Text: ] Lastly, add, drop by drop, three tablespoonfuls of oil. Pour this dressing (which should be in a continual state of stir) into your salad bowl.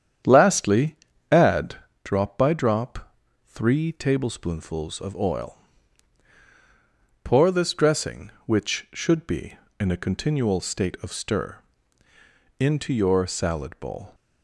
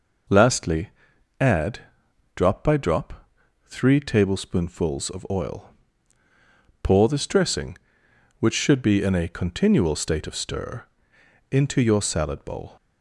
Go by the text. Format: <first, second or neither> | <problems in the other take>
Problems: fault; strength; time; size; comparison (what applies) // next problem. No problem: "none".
second | starts louder than the rest; strong; until 1.9 s; 9 dB